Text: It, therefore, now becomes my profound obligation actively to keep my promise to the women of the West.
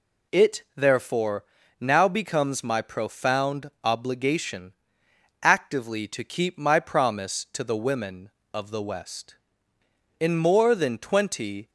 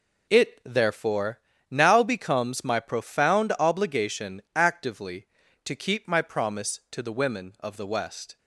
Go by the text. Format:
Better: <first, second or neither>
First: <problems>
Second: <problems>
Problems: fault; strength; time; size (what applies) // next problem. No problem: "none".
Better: second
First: pauses between "obligation" and "actively"; noticeable; at 4.7 s; 0.68 s long // goes on to say "In more than twenty"; from 10.1 s on; 1.5 s long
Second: none